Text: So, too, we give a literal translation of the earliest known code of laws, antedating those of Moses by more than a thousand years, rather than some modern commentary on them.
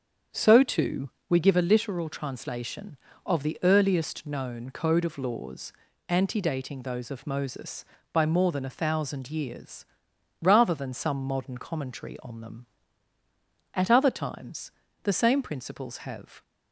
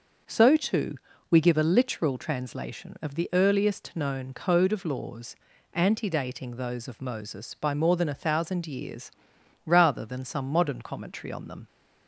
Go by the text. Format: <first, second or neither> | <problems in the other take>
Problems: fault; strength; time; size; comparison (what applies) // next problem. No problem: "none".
second | starts louder than the rest; strong; until 1.4 s; 7.5 dB; also in the second // goes on to say "At other times the same principles have"; strong; from 13.7 s on; 2.6 s long